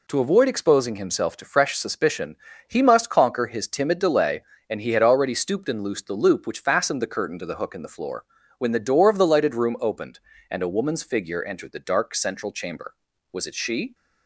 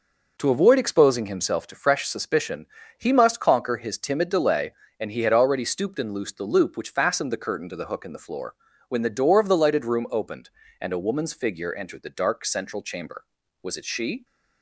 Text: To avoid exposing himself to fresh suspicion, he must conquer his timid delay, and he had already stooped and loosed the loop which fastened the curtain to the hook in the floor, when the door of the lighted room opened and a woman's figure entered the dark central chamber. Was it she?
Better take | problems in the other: first | starts louder than the rest; noticeable; until 1.6 s; 5 dB

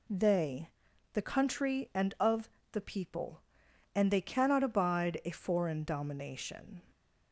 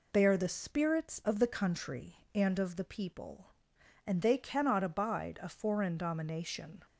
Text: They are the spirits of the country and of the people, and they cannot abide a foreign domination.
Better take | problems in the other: second | skips "are the spirits of"; at 0.9 s // pauses between "of" and "the"; slight; at 2.4 s; 0.24 s long

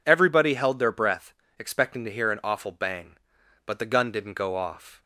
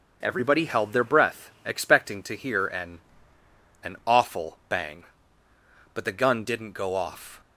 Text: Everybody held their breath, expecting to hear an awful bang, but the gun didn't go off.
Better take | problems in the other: first | starts louder than the rest; until 1.2 s; 6 dB // says "an" twice; at 3.8 s

